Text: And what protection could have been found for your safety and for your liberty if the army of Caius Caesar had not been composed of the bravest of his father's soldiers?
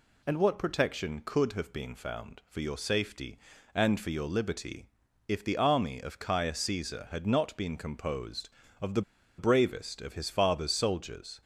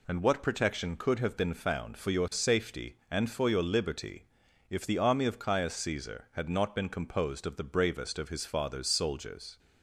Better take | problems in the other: second | pauses between "liberty" and "if"; at 4.8 s; 0.42 s long; noticeable in the second // pauses between "the" and "bravest"; at 9.0 s; 0.37 s long

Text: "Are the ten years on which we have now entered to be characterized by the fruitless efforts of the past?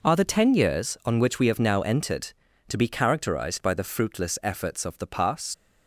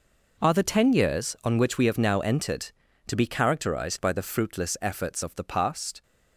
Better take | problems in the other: second | leaves "past" unfinished; at 5.5 s; 105 ms

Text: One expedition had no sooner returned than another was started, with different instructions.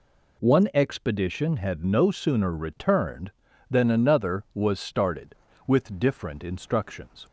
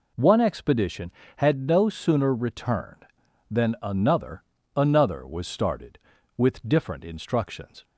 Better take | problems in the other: first | says "another" twice; at 4.7 s

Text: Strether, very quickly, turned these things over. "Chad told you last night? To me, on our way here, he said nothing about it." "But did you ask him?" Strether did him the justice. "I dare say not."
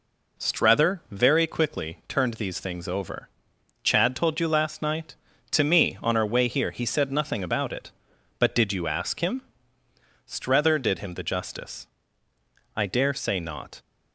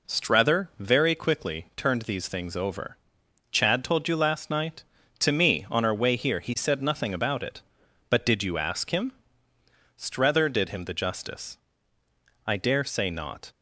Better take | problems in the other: neither | none

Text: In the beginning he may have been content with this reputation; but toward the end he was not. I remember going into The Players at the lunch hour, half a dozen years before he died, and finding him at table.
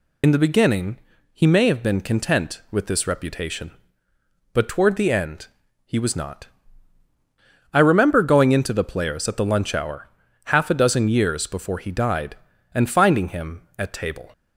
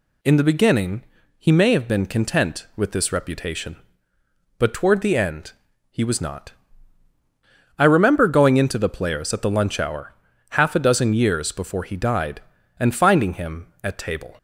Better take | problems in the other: second | loses the start of "In"; at 0.2 s; 55 ms // pauses between "beginning" and "he"; slight; at 0.9 s; 0.36 s long; slight in the second // pauses between "end" and "he"; slight; at 5.4 s; 0.36 s long; slight in the second

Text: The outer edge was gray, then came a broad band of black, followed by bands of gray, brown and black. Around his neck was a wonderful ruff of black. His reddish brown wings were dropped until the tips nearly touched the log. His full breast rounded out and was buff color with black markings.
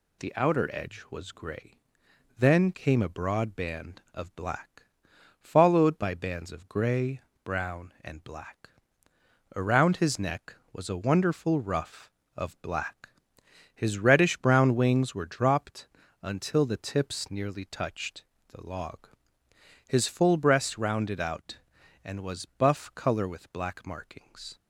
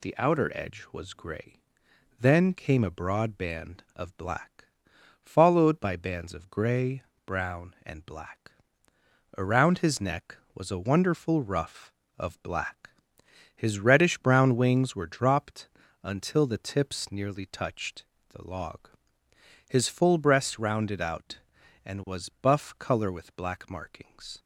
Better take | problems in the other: neither | pauses between "dropped" and "until"; slight; the same in both // pauses between "touched" and "the"; slight; the same in both

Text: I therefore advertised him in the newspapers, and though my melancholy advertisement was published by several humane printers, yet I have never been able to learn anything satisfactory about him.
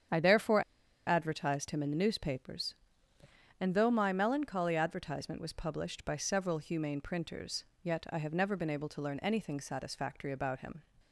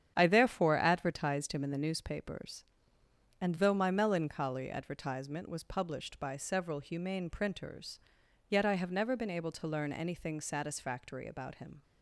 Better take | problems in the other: second | starts louder than the rest; strong; until 1.5 s; 8.5 dB; strong in the second // pauses between "therefore" and "advertised"; at 0.6 s; 0.44 s long

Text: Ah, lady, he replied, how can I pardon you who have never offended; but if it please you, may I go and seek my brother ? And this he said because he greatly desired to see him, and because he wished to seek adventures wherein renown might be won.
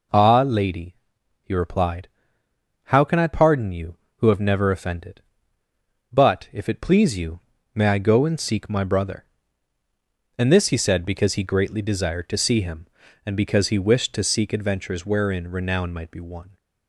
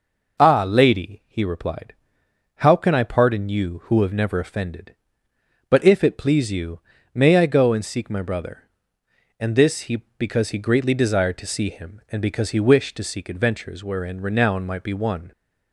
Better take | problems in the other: first | skips "said"; at 10.1 s

